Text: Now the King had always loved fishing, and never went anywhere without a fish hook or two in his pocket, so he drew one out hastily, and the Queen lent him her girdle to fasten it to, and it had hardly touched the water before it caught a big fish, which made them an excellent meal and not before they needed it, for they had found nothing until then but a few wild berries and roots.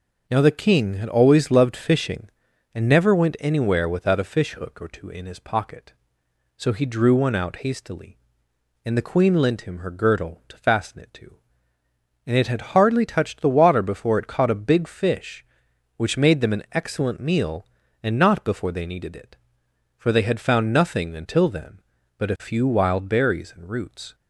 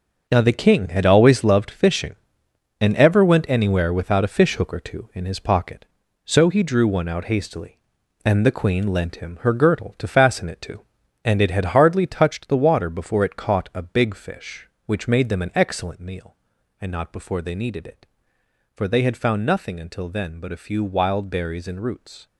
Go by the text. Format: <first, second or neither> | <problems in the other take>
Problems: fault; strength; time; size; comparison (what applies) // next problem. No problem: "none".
first | starts louder than the rest; noticeable; until 1.2 s; 6 dB // says "ever" for "never"; at 2.9 s